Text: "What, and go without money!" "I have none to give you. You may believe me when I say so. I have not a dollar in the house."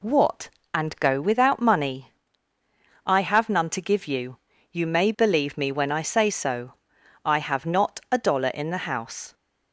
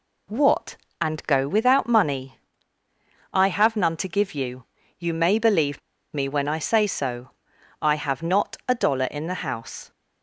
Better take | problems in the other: first | pauses between "believe" and "me"; slight; at 5.8 s; 0.34 s long

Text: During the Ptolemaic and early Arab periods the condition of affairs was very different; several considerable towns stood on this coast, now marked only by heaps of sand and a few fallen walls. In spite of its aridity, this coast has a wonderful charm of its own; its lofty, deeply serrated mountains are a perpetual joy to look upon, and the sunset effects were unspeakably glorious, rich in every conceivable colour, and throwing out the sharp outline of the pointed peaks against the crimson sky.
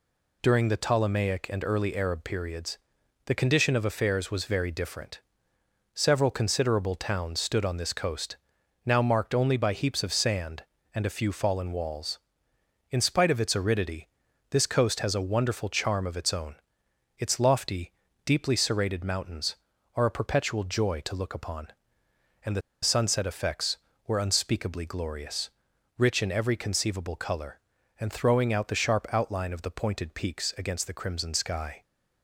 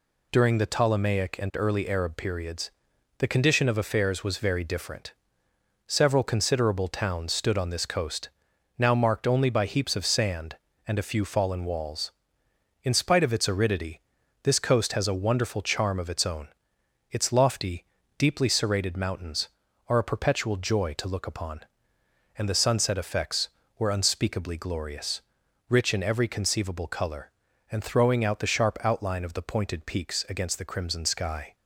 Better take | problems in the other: second | pauses between "periods" and "the"; noticeable; at 2.7 s; 0.48 s long; noticeable in the second // pauses between "the" and "sunset"; slight; at 22.6 s; 0.21 s long

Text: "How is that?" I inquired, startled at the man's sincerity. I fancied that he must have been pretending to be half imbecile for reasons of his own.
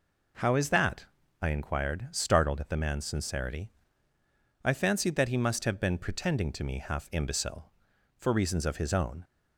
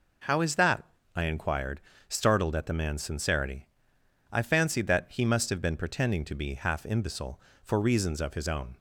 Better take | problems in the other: second | says "me" for "be"; at 6.6 s

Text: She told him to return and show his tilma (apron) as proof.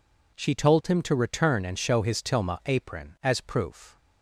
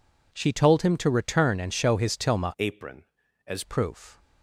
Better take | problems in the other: first | changes voice from "apron" to "as"; from 2.5 to 3.6 s; 1.1 s long

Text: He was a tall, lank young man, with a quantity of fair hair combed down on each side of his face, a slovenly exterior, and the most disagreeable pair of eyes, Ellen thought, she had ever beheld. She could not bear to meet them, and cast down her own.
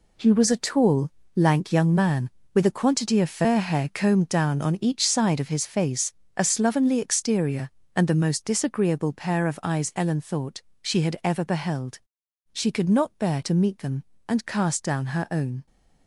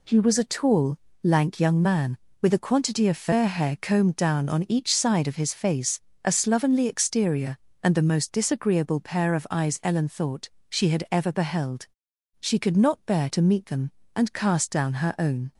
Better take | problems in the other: second | gets quieter; strong; throughout; 9.5 dB

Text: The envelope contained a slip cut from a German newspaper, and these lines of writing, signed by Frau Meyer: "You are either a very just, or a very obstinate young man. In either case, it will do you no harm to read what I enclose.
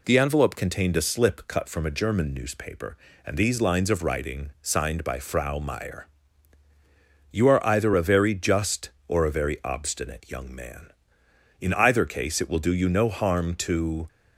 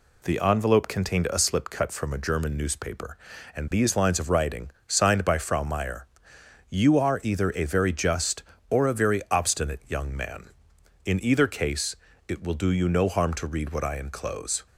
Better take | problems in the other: second | stops before "read what I enclose"; at 14.0 s

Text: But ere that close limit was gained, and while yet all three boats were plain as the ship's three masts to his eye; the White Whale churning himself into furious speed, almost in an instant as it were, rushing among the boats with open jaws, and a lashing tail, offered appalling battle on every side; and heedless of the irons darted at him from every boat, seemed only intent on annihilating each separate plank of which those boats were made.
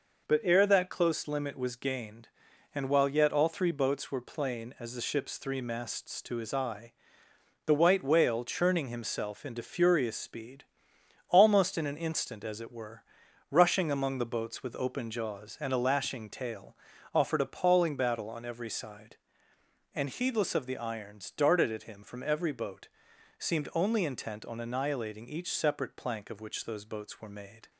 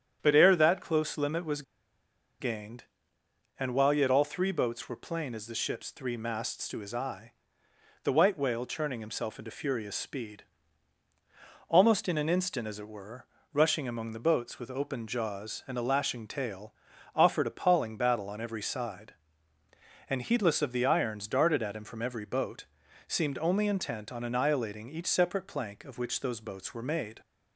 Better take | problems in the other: first | starts louder than the rest; strong; until 1.2 s; 9 dB // pauses between "was" and "gained"; noticeable; at 1.6 s; 0.78 s long

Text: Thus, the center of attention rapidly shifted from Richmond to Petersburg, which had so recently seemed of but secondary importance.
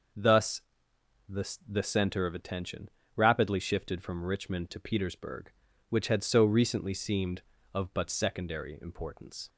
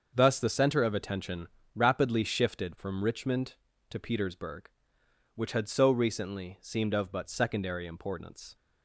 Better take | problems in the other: second | starts louder than the rest; until 2.0 s; 6.5 dB; also in the second // says "the" twice; at 1.6 s // pauses between "attention" and "rapidly"; slight; at 2.8 s; 0.26 s long; slight in the second

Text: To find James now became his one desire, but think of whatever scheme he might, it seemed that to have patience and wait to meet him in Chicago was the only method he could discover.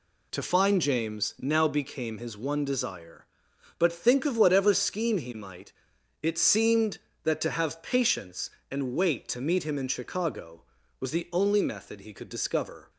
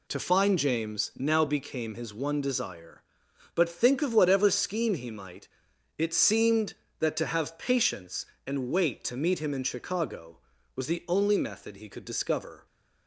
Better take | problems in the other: neither | none

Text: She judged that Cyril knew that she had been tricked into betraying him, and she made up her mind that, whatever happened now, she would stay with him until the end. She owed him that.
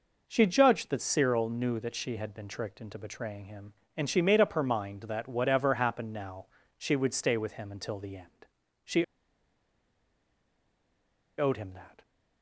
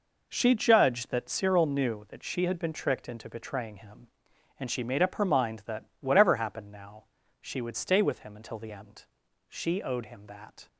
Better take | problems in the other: second | pauses between "She" and "owed"; strong; at 9.0 s; 2.3 s long

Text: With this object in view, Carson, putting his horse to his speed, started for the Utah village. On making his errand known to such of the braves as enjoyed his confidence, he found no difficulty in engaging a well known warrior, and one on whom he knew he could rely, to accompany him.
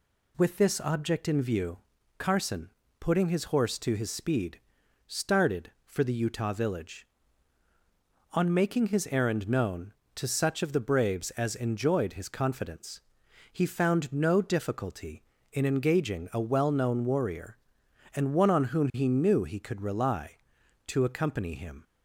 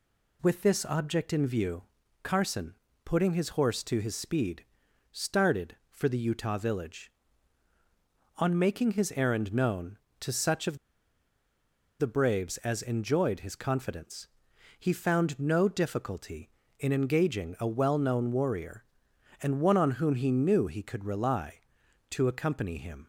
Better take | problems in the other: first | pauses between "of" and "the"; at 10.7 s; 1.2 s long

